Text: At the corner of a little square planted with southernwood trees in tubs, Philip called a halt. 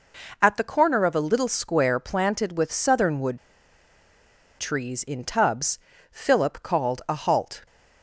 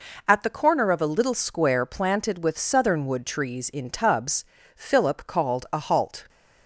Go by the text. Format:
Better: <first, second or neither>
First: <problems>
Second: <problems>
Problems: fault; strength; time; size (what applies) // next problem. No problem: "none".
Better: second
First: pauses between "southernwood" and "trees"; at 3.3 s; 1.2 s long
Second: none